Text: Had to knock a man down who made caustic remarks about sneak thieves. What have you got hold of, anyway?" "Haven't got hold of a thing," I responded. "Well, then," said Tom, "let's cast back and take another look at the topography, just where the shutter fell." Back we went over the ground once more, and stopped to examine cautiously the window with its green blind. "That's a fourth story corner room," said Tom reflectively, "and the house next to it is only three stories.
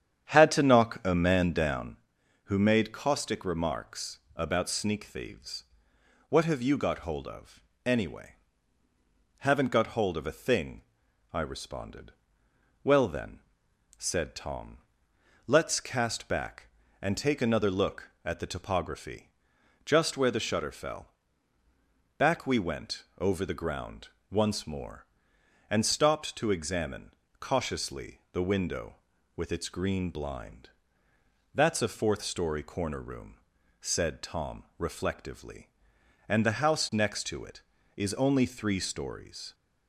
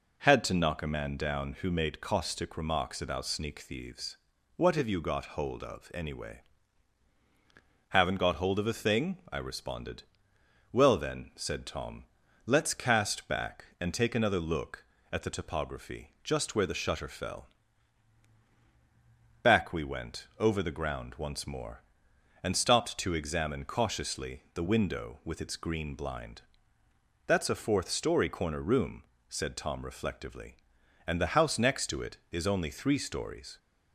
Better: second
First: starts louder than the rest; strong; until 2.0 s; 9 dB // pauses between "remarks" and "about"; slight; at 4.1 s; 0.18 s long // pauses between "went" and "over"; slight; at 23.0 s; 0.16 s long // pauses between "ground" and "once"; slight; at 24.0 s; 0.24 s long // pauses between "examine" and "cautiously"; slight; at 27.1 s; 0.26 s long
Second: none

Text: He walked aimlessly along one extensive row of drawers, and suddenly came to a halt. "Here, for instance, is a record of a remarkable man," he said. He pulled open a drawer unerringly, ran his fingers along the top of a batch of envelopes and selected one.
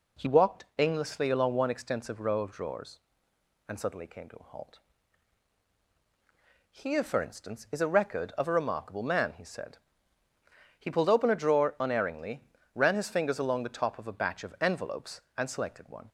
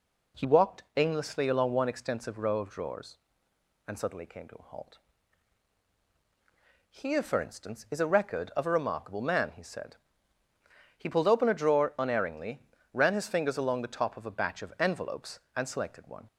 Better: neither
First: none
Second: none

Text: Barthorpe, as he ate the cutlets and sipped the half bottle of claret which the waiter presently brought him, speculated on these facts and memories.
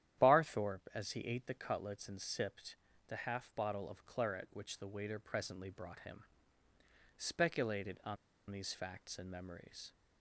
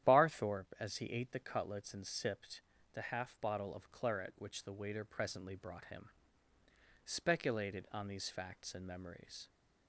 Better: second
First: starts louder than the rest; strong; until 1.2 s; 11 dB // pauses between "sipped" and "the"; slight; at 2.7 s; 0.32 s long // pauses between "on" and "these"; slight; at 8.1 s; 0.34 s long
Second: starts louder than the rest; strong; until 1.1 s; 11 dB // pauses between "sipped" and "the"; slight; at 2.6 s; 0.32 s long

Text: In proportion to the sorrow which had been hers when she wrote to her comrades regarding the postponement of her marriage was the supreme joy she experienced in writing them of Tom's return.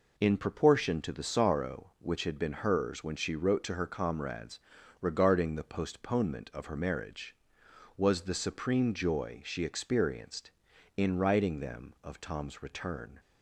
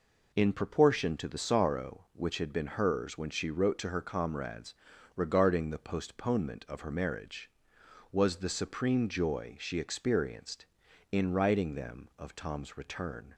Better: neither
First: pauses between "comrades" and "regarding"; at 4.5 s; 0.42 s long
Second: pauses between "comrades" and "regarding"; at 4.7 s; 0.42 s long

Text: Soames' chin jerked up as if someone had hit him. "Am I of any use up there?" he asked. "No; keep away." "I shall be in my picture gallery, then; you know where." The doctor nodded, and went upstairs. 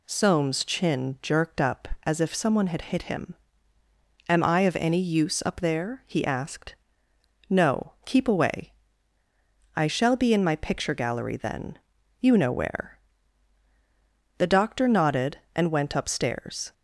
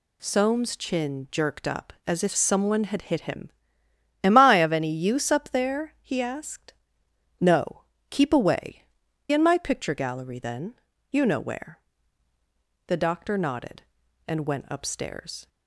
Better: first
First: none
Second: skips "I shall be"; at 9.0 s

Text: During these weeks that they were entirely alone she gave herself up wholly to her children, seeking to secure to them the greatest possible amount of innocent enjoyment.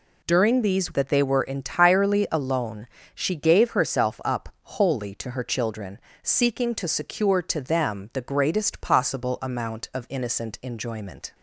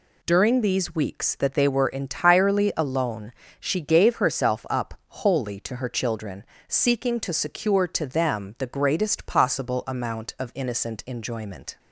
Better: second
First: skips "weeks"; at 0.9 s // pauses between "alone" and "she"; slight; at 2.8 s; 0.28 s long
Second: pauses between "alone" and "she"; slight; at 3.3 s; 0.28 s long

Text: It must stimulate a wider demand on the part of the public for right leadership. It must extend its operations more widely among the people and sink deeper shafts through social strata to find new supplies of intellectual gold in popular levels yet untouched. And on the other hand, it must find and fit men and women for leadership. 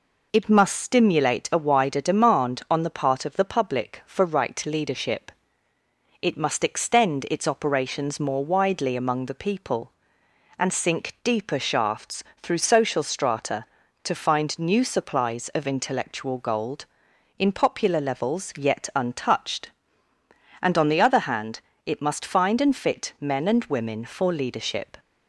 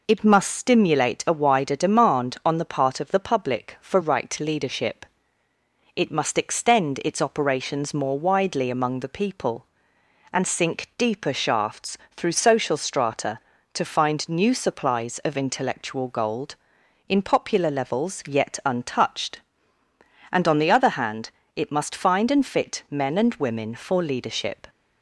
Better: neither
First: pauses between "shafts" and "through"; slight; at 12.2 s; 0.20 s long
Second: pauses between "shafts" and "through"; slight; at 11.9 s; 0.20 s long

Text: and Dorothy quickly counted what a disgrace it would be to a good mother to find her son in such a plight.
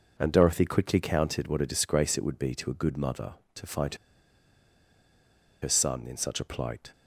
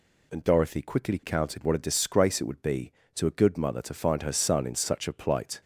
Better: second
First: pauses between "find" and "her"; strong; at 3.9 s; 1.6 s long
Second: none

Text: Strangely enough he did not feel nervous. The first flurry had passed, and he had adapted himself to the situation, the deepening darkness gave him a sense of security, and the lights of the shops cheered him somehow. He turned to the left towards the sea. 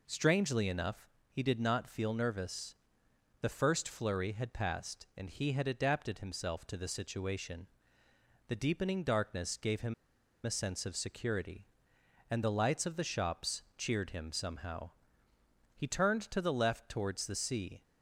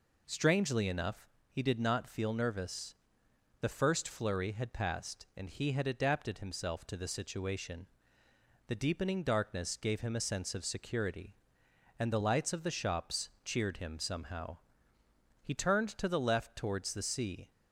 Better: second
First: pauses between "enough" and "he"; slight; at 1.0 s; 0.22 s long // pauses between "him" and "a"; noticeable; at 9.9 s; 0.50 s long // pauses between "shops" and "cheered"; slight; at 13.6 s; 0.16 s long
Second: pauses between "enough" and "he"; slight; at 1.2 s; 0.22 s long // pauses between "shops" and "cheered"; slight; at 13.2 s; 0.16 s long

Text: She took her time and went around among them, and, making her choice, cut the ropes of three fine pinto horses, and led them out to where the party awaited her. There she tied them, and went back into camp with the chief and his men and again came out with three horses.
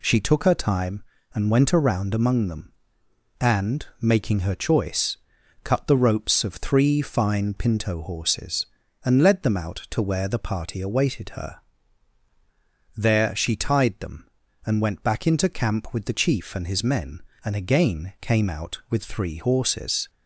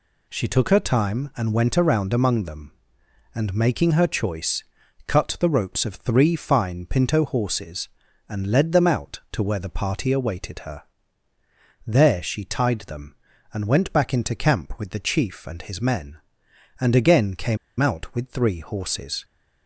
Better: first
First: none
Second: pauses between "came" and "out"; slight; at 17.5 s; 0.22 s long

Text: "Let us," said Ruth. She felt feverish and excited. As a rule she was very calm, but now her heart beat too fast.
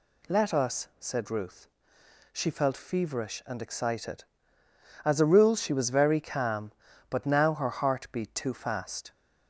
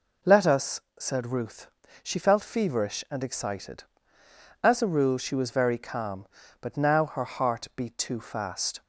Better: neither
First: none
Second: none

